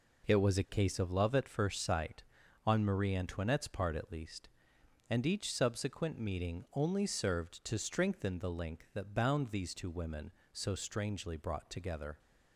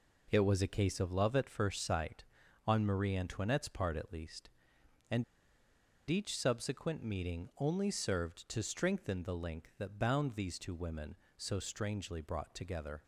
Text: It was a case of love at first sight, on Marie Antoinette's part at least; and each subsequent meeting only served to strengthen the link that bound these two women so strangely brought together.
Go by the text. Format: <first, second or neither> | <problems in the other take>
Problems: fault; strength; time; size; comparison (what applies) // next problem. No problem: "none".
first | pauses between "and" and "each"; noticeable; at 5.2 s; 0.84 s long